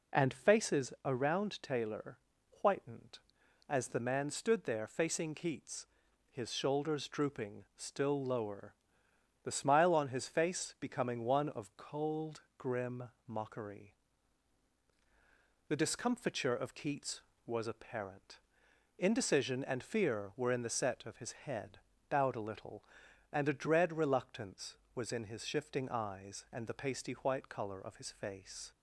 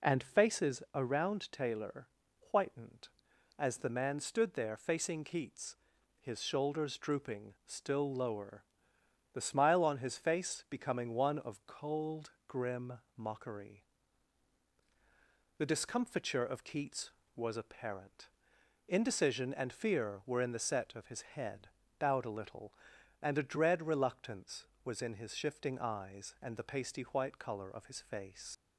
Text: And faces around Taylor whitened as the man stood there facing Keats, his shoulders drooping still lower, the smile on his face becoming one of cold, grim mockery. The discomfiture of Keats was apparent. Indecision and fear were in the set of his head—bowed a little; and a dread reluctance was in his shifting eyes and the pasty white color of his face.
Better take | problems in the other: first | pauses between "Taylor" and "whitened"; at 2.0 s; 0.42 s long; also in the first // pauses between "grim" and "mockery"; slight; at 12.9 s; 0.22 s long; slight in the first // leaves "face" unfinished; at 28.5 s; 55 ms

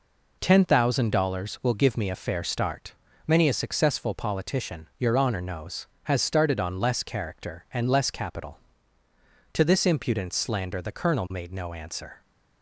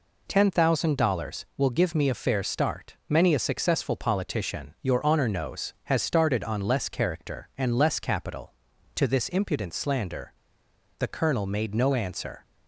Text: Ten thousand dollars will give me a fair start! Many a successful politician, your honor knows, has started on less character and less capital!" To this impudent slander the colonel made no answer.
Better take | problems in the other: first | pauses between "slander" and "the"; noticeable; at 10.3 s; 0.65 s long

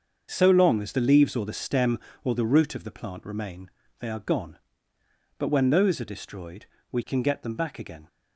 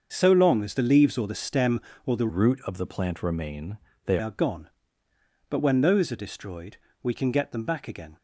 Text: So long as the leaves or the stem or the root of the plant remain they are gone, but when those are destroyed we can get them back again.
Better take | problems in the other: first | starts louder than the rest; until 1.1 s; 6.5 dB; also in the first // changes voice from "root" to "they"; from 2.2 to 4.1 s; 1.9 s long // pauses between "remain" and "they"; slight; at 3.7 s; 0.28 s long; slight in the first // pauses between "destroyed" and "we"; slight; at 6.7 s; 0.24 s long; slight in the first

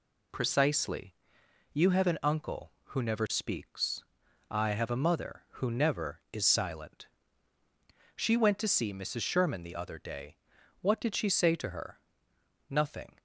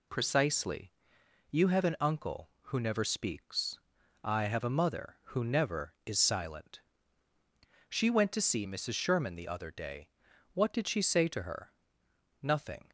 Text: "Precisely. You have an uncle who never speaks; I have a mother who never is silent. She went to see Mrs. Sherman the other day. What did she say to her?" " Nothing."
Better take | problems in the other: neither | none

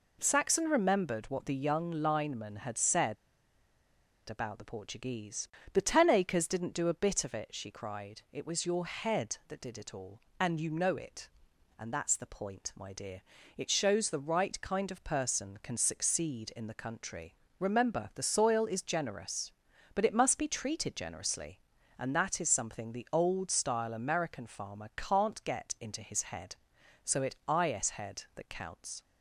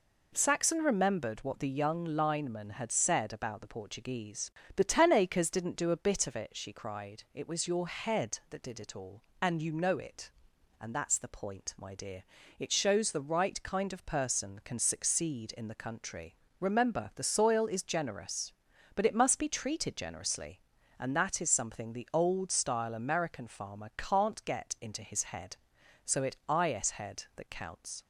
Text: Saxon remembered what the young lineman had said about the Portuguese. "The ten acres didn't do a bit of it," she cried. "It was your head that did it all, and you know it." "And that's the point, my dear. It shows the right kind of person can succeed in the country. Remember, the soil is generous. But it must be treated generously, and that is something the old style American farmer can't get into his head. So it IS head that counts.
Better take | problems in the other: second | pauses between "said" and "about"; at 3.1 s; 1.1 s long

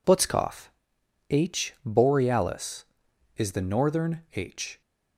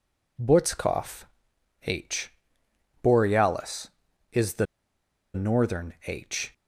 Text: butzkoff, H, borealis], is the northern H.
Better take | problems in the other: first | pauses between "the" and "northern"; noticeable; at 4.6 s; 0.69 s long

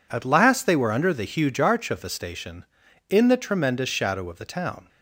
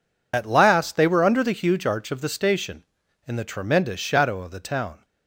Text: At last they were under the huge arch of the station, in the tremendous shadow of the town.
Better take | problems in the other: first | loses the start of "At"; at 0.3 s; 60 ms

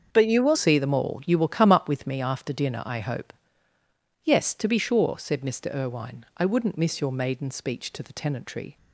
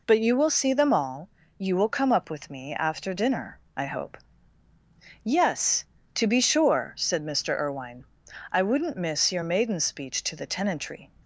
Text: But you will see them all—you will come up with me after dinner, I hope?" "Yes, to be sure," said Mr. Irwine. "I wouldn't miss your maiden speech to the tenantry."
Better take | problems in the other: second | starts louder than the rest; until 1.1 s; 7 dB // changes voice at "see"; from 0.5 s on; 8.2 s long

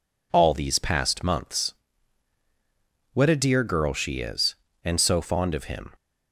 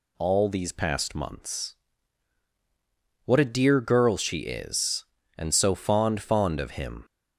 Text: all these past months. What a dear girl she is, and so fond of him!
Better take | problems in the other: first | says "fond" twice; at 6.2 s

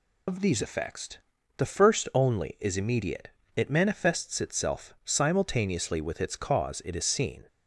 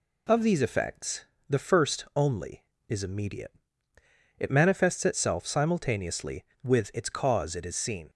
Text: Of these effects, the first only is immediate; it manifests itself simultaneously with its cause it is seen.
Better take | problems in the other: second | loses the start of "Of"; at 0.2 s; 85 ms

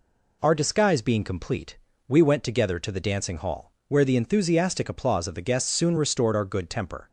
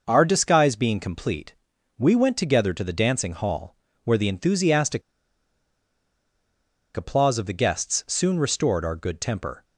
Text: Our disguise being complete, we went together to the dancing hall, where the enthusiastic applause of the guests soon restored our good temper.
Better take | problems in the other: first | pauses between "enthusiastic" and "applause"; strong; at 5.0 s; 1.9 s long

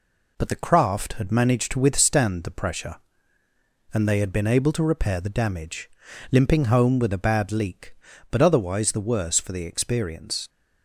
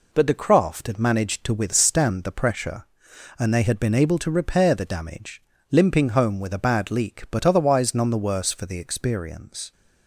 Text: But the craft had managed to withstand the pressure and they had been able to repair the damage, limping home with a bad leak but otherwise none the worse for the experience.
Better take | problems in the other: second | skips "none"; at 8.9 s

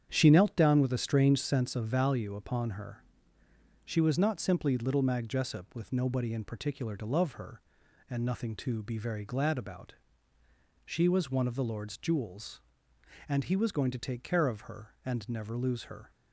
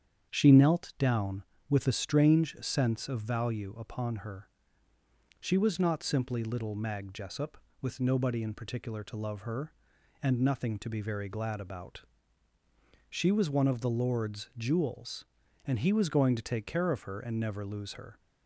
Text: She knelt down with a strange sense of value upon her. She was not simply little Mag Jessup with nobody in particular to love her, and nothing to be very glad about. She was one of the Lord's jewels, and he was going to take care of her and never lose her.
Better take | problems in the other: neither | starts louder than the rest; strong; the same in both

